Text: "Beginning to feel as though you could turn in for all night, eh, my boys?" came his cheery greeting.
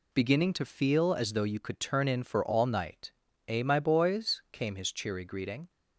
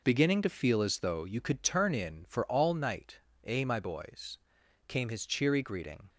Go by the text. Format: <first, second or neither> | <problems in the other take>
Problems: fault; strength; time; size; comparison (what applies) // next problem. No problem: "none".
neither | none